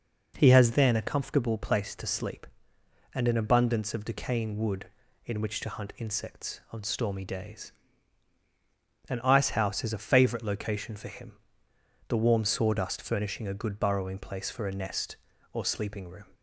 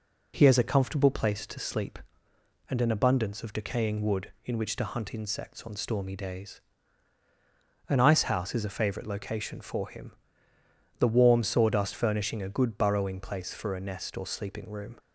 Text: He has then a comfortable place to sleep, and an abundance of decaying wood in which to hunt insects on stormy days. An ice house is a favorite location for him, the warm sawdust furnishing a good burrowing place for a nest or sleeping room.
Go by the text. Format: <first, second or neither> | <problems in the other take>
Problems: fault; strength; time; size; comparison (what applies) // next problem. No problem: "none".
first | skips "then"; at 0.5 s